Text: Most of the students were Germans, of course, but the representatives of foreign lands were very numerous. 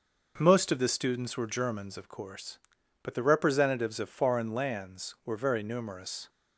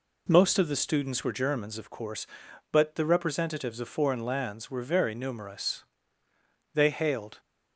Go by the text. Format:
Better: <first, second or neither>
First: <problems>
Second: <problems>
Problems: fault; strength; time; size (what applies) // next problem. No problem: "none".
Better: first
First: none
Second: goes on to say "They hailed"; noticeable; from 6.7 s on; 0.66 s long